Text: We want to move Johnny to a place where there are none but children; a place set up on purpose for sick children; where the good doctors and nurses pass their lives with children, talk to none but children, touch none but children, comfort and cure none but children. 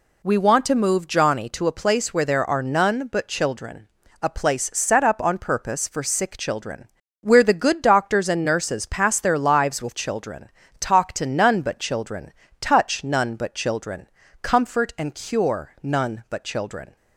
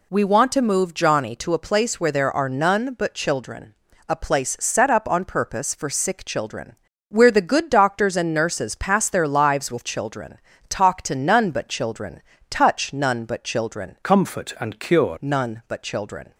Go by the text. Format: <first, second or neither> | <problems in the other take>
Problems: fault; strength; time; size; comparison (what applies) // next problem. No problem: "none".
first | changes voice from "comfort" to "cure"; from 14.0 to 15.1 s; 1.1 s long